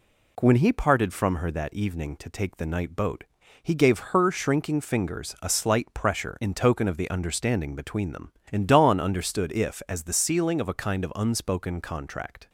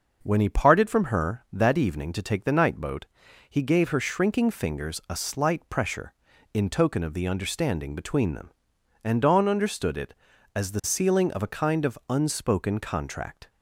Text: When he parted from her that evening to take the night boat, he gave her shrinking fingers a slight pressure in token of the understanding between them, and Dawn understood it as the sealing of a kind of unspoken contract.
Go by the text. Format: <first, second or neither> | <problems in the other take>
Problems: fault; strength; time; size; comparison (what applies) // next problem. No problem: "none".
second | says "if" for "it"; at 9.5 s